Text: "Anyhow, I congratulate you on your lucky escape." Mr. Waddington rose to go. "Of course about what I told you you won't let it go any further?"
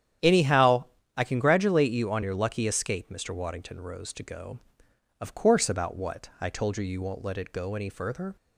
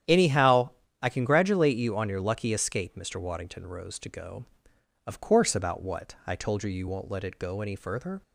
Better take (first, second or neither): neither